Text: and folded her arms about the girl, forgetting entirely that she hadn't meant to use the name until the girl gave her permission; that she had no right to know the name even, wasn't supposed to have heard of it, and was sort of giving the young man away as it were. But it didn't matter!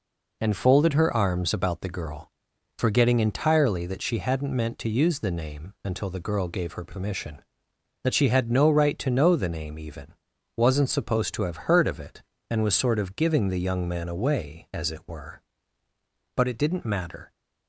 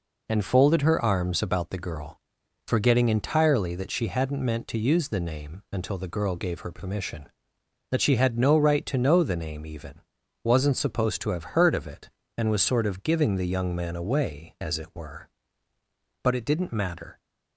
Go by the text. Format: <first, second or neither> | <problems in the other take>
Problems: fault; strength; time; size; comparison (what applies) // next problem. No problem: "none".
neither | none